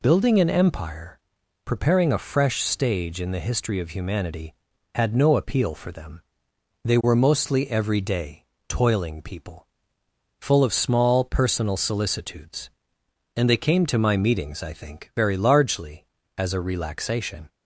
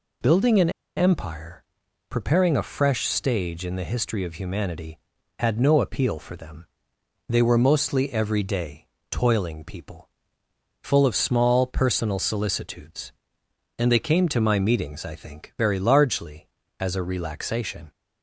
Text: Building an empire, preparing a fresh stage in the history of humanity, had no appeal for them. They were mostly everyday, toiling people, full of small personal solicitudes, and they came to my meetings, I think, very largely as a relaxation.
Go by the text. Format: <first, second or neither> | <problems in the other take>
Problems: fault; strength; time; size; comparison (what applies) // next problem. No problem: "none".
first | pauses between "an" and "empire"; slight; at 0.7 s; 0.26 s long